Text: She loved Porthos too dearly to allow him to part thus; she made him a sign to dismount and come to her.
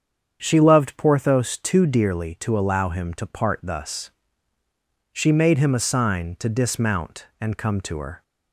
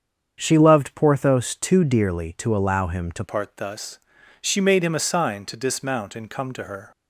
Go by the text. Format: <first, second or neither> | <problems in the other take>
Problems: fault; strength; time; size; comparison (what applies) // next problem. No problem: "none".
first | starts louder than the rest; strong; until 1.4 s; 7.5 dB; strong in the first // changes voice at "part"; from 3.2 s on; 3.7 s long